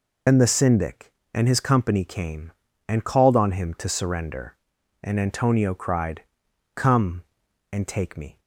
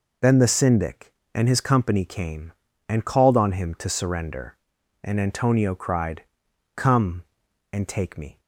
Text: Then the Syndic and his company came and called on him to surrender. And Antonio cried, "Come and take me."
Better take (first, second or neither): second